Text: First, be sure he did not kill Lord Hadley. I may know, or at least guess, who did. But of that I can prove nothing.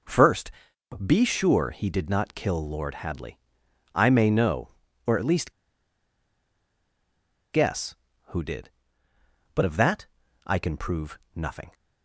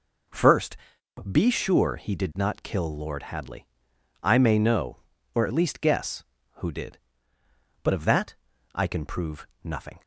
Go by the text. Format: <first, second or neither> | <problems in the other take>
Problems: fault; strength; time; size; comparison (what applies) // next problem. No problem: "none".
second | pauses between "least" and "guess"; strong; at 5.5 s; 2.0 s long // pauses between "that" and "I"; at 10.0 s; 0.40 s long; also in the second // pauses between "prove" and "nothing"; slight; at 11.1 s; 0.16 s long; slight in the second